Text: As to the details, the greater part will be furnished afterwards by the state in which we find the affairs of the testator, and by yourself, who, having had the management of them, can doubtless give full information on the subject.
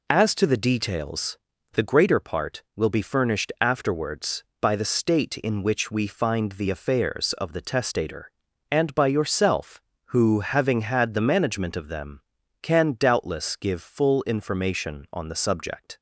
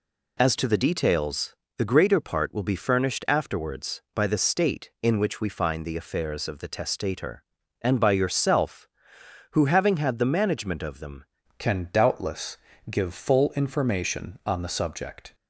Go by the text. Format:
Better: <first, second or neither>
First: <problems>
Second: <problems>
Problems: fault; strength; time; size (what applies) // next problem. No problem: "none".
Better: first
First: none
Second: changes voice at "can"; from 11.5 s on; 3.8 s long // pauses between "doubtless" and "give"; slight; at 12.5 s; 0.34 s long